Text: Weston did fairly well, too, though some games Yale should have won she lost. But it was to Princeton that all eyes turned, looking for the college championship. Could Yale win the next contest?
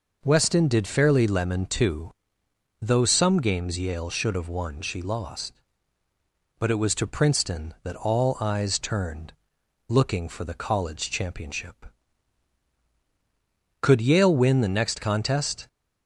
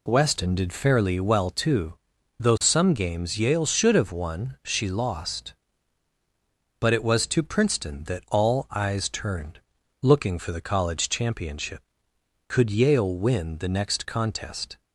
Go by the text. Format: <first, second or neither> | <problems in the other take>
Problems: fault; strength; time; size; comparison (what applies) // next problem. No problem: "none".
second | says "lemon" for "well"; at 1.2 s